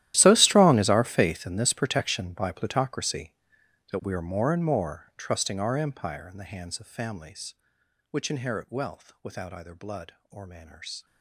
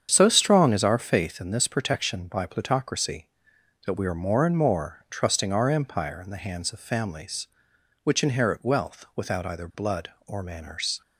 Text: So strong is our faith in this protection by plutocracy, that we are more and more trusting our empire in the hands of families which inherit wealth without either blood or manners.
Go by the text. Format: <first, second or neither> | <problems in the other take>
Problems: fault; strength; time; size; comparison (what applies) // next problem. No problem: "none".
second | gets quieter; strong; throughout; 19 dB // starts louder than the rest; strong; until 1.1 s; 13.5 dB; strong in the second